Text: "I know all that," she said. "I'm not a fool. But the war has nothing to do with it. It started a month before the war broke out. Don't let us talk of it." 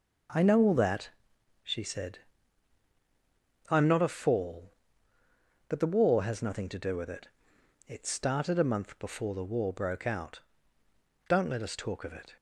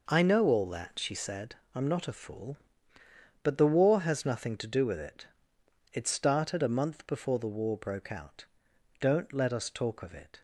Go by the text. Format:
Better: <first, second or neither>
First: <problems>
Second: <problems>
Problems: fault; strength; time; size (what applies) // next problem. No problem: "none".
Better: second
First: says "fall" for "fool"; at 4.0 s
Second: none